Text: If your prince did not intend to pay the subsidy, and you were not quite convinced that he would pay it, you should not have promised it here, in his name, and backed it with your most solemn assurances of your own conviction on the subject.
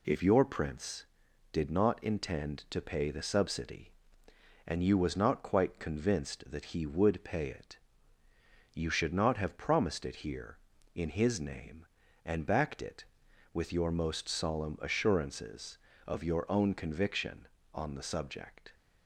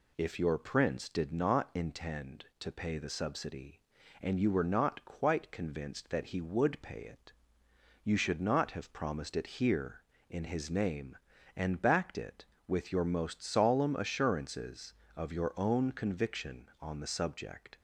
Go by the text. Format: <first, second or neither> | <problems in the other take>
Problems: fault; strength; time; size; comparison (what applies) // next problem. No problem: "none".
second | says "was" for "were"; at 4.9 s